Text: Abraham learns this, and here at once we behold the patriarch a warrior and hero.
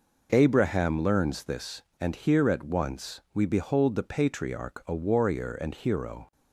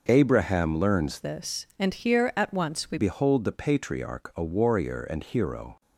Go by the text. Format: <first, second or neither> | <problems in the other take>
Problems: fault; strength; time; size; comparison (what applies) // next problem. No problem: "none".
first | changes voice from "this" to "we"; from 1.2 to 2.9 s; 1.7 s long